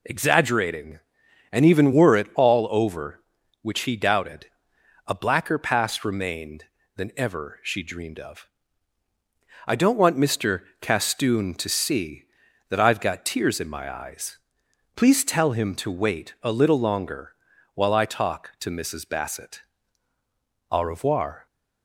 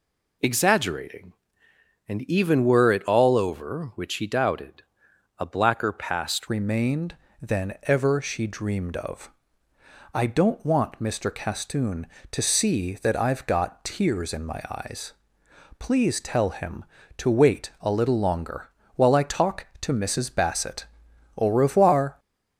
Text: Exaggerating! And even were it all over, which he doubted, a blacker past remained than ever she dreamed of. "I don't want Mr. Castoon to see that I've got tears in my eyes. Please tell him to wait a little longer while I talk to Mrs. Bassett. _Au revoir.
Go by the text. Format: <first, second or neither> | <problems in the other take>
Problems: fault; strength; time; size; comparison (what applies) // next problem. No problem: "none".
first | changes voice at "remained"; from 6.4 s on; 15.7 s long // pauses between "longer" and "while"; slight; at 18.6 s; 0.30 s long; also in the first